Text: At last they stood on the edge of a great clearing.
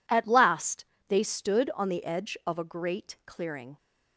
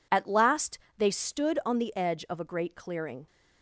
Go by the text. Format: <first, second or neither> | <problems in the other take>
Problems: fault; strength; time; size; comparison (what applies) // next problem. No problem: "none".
neither | pauses between "last" and "they"; slight; the same in both